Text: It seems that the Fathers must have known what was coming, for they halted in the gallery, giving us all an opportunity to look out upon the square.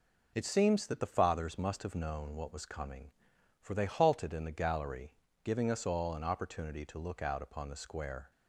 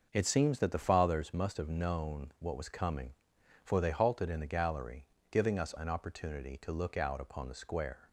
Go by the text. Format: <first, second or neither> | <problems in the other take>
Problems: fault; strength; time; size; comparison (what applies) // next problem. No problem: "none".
first | starts louder than the rest; noticeable; until 1.1 s; 6 dB // skips "all"; at 5.7 s